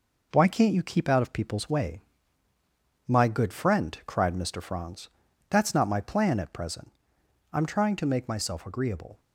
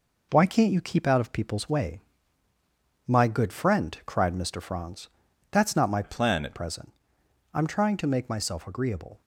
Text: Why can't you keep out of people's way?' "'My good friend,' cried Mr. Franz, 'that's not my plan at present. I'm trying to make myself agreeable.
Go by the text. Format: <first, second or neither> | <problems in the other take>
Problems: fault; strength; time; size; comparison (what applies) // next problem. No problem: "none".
first | changes voice from "plan" to "at"; from 6.0 to 6.5 s; 0.5 s long